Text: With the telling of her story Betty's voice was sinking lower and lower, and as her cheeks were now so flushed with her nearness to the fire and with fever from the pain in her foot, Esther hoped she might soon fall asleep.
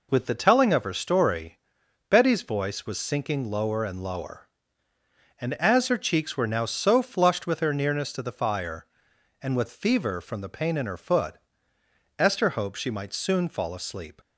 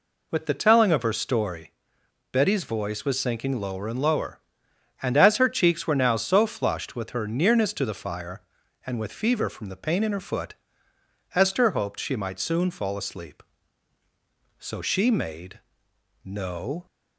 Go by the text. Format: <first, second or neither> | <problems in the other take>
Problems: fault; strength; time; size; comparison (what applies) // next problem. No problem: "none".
first | pauses between "story" and "Betty's"; noticeable; at 1.7 s; 0.60 s long; noticeable in the first // goes on to say "So she made no"; strong; from 14.5 s on; 2.2 s long